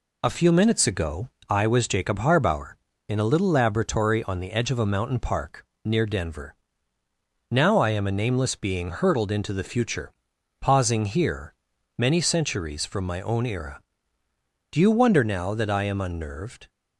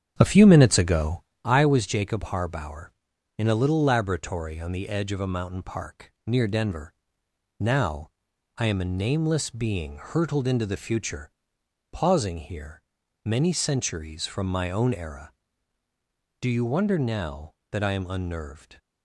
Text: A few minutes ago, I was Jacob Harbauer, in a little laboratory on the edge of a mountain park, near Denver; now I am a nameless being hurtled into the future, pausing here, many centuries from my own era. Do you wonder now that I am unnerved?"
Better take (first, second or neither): first